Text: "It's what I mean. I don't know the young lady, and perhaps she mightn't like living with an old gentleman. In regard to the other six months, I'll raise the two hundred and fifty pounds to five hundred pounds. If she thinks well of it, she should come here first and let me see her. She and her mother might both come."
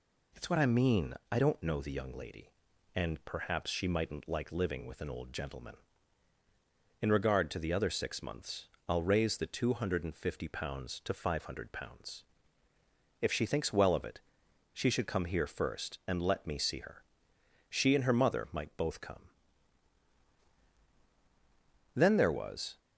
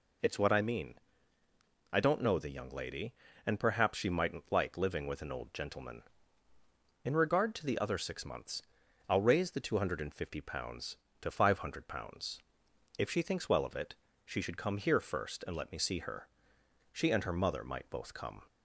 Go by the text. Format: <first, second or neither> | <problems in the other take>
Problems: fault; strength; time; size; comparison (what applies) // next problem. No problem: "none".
second | goes on to say "Then there was"; noticeable; from 21.9 s on; 0.84 s long